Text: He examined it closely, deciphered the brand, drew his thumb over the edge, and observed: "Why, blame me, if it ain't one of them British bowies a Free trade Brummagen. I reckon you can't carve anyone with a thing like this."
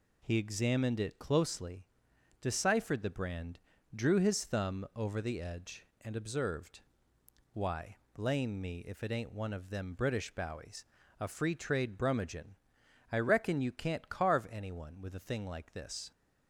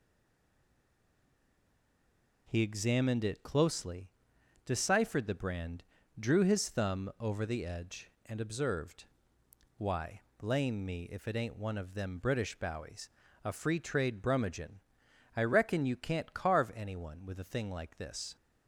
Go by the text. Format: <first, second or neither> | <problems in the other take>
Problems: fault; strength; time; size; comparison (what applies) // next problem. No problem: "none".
first | stays silent before the first word; until 2.4 s; 2.4 s long // pauses between "bowies" and "a"; slight; at 13.0 s; 0.34 s long; slight in the first